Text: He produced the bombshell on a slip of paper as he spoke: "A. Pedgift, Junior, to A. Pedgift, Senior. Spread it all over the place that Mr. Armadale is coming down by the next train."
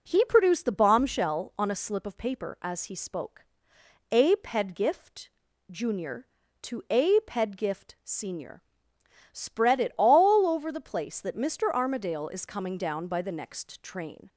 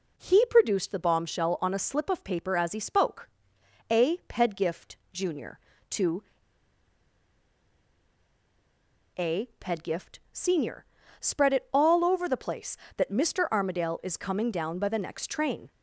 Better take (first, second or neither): first